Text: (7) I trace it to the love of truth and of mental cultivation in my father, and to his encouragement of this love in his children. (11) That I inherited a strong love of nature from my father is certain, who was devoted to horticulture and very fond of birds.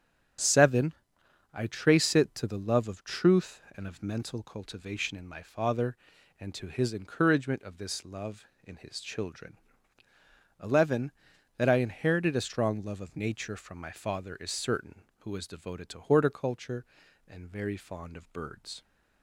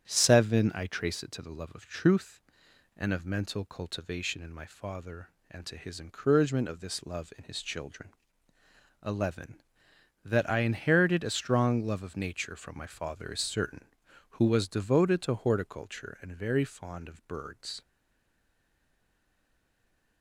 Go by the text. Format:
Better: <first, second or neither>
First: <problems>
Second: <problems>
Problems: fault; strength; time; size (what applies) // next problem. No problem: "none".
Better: first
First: starts louder than the rest; strong; until 2.0 s; 8 dB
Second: starts louder than the rest; strong; until 1.1 s; 8 dB // stays silent after the last word; from 17.8 s on; 2.4 s long